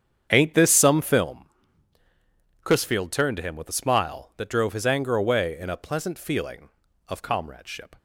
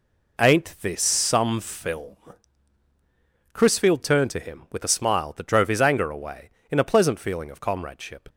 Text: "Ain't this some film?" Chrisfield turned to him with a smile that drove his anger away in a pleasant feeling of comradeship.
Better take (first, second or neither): second